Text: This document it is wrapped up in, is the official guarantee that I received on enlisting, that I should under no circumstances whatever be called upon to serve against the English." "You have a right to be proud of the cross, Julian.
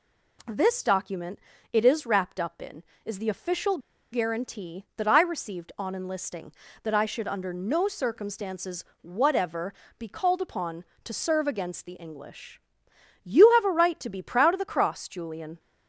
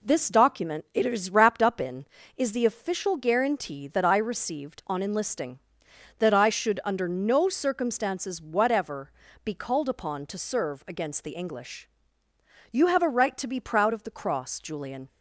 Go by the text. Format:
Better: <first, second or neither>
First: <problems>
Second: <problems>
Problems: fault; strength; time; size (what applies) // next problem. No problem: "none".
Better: second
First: pauses between "document" and "it"; slight; at 1.3 s; 0.34 s long // pauses between "official" and "guarantee"; slight; at 3.7 s; 0.34 s long // pauses between "circumstances" and "whatever"; slight; at 8.8 s; 0.20 s long // pauses between "whatever" and "be"; slight; at 9.7 s; 0.28 s long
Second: pauses between "whatever" and "be"; slight; at 9.1 s; 0.34 s long